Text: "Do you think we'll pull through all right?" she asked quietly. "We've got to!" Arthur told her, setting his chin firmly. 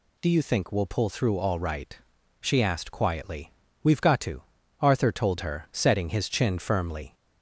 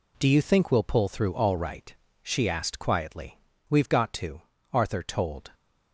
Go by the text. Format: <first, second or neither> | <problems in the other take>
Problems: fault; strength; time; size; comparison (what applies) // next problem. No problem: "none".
first | stops before "her setting his chin firmly"; at 5.5 s